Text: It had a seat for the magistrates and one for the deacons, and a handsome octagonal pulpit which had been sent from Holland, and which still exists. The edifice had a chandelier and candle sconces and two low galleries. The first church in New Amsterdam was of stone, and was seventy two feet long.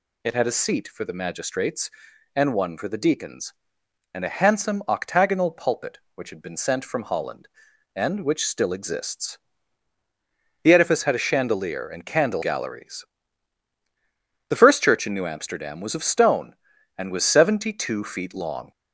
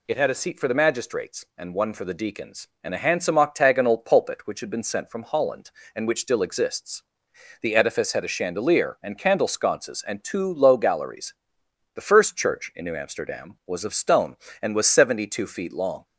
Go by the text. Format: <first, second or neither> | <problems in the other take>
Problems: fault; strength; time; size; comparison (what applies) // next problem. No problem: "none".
second | skips "sconces and two low"; at 12.4 s